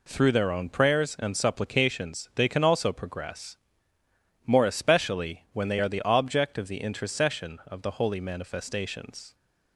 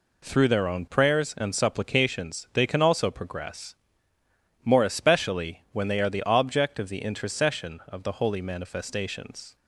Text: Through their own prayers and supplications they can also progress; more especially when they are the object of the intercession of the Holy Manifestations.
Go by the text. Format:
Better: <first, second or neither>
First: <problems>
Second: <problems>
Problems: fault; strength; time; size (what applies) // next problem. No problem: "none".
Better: neither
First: none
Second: none